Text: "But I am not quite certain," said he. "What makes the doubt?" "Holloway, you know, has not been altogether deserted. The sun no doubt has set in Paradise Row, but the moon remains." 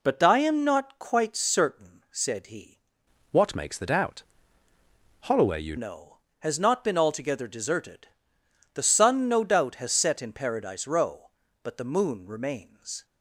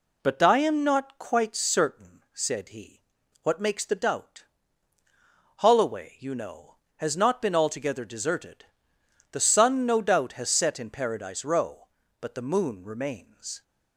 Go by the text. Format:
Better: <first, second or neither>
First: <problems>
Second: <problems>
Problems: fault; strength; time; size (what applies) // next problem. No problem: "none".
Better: second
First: changes voice from "What" to "you"; from 3.3 to 5.7 s; 2.4 s long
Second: none